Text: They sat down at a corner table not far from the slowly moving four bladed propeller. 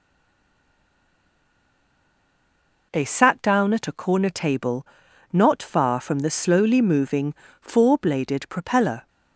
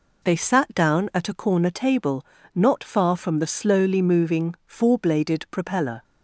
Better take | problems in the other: second | stays silent before the first word; strong; until 2.9 s; 2.9 s long // pauses between "table" and "not"; at 4.8 s; 0.44 s long; slight in the second // pauses between "moving" and "four"; slight; at 7.3 s; 0.26 s long

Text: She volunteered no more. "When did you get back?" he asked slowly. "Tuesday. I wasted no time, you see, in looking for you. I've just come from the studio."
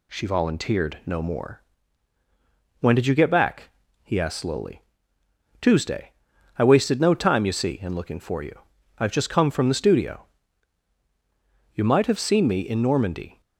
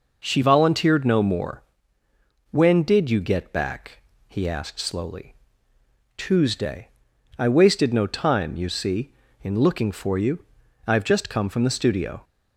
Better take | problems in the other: second | goes on to say "You might have seen me in Normandy"; from 11.7 s on; 1.6 s long

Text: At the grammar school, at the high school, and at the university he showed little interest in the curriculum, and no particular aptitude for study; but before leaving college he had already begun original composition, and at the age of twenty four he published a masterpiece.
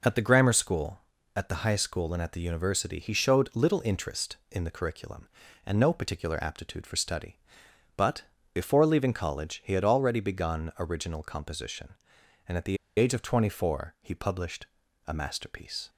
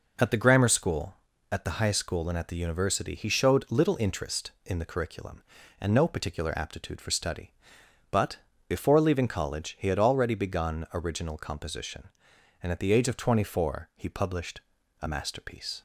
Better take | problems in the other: second | pauses between "but" and "before"; slight; at 8.2 s; 0.32 s long; slight in the second // pauses between "the" and "age"; slight; at 12.7 s; 0.22 s long // pauses between "published" and "a"; at 14.6 s; 0.40 s long; also in the second

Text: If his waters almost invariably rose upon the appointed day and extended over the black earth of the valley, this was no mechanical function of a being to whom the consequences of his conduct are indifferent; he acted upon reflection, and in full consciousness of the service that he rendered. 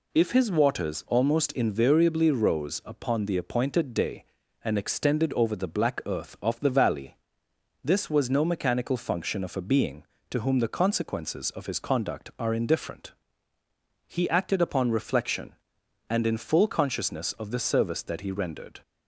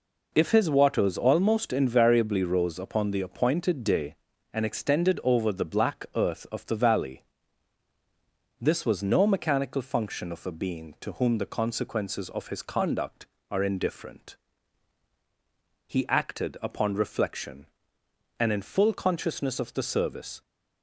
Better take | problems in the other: first | stops before "that he rendered"; at 20.4 s

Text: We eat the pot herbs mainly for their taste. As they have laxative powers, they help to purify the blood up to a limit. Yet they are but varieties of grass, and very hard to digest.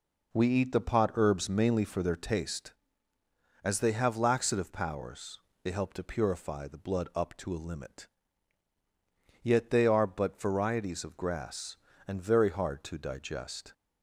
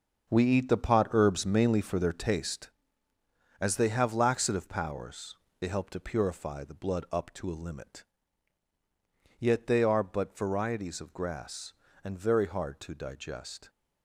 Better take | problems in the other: first | gets quieter; strong; throughout; 10 dB

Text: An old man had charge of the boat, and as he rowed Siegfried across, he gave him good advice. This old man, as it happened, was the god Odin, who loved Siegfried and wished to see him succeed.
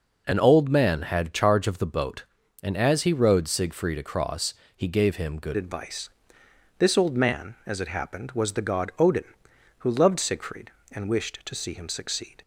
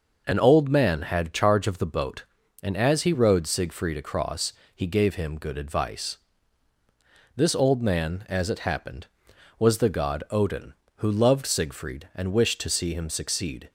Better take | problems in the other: second | changes voice at "advice"; from 5.5 s on; 6.9 s long

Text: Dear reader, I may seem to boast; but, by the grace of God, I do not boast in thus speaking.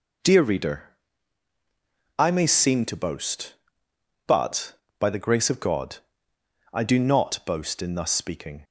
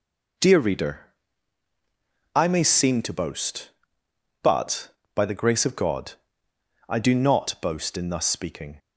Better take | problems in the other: neither | none

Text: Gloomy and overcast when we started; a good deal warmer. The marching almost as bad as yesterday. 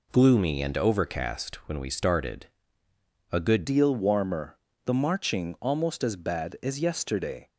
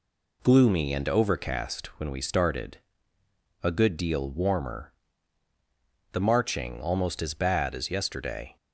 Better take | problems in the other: second | changes voice at "deal"; from 3.6 s on; 3.9 s long

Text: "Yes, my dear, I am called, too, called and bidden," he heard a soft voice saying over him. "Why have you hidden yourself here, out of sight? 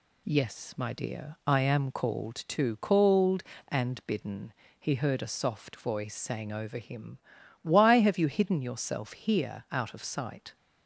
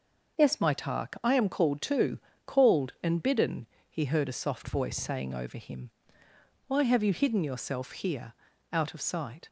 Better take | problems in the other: first | starts louder than the rest; noticeable; until 1.4 s; 6 dB // says "tark" for "dear"; at 0.7 s

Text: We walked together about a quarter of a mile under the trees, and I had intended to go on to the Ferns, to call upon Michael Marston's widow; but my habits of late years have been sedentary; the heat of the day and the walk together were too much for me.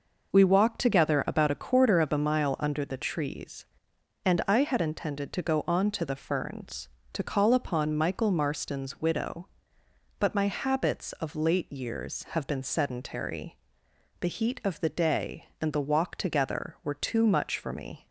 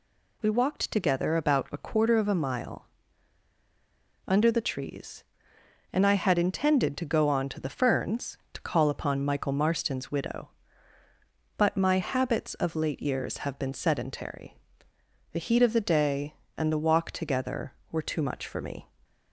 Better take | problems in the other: first | pauses between "mile" and "under"; strong; at 2.8 s; 1.4 s long

